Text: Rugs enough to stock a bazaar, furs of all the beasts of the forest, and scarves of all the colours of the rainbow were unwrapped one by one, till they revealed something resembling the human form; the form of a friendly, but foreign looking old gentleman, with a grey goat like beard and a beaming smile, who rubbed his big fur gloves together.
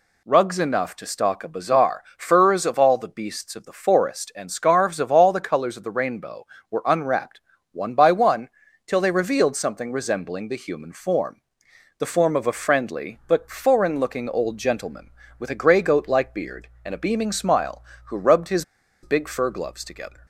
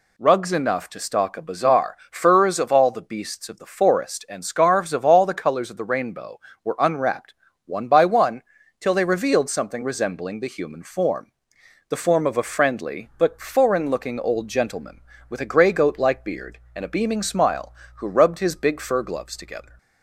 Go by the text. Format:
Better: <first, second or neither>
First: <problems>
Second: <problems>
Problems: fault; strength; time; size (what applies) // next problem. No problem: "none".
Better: second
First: pauses between "unwrapped" and "one"; slight; at 7.4 s; 0.32 s long // pauses between "his" and "big"; at 18.6 s; 0.39 s long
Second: pauses between "unwrapped" and "one"; slight; at 7.3 s; 0.32 s long